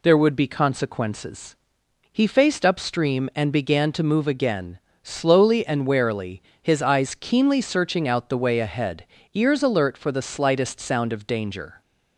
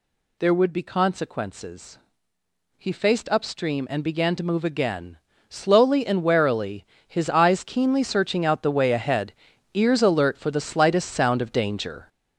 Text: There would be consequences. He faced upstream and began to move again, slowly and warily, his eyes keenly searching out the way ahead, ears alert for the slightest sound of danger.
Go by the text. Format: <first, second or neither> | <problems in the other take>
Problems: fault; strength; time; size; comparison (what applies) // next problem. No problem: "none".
first | gets louder; strong; throughout; 7 dB